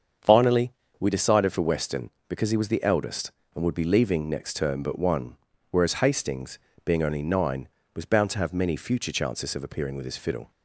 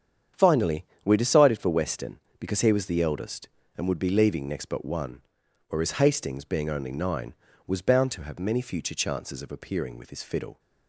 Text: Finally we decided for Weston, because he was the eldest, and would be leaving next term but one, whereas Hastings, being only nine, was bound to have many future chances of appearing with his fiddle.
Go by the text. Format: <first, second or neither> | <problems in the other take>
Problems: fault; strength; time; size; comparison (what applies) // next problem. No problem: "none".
first | starts louder than the rest; strong; until 1.5 s; 8.5 dB; strong in the first // pauses between "Finally" and "we"; slight; at 0.8 s; 0.20 s long; slight in the first // skips "term"; at 4.6 s